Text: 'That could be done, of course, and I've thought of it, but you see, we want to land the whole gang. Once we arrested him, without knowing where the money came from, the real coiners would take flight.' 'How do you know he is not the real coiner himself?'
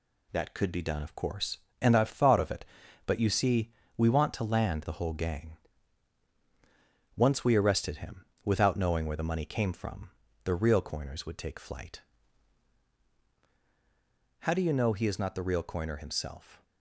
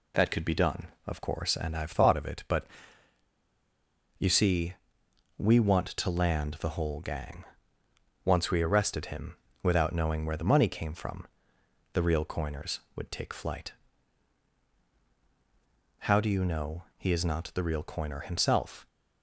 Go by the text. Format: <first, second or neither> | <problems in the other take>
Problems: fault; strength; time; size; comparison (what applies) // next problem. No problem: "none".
first | pauses between "but" and "you"; strong; at 2.6 s; 1.5 s long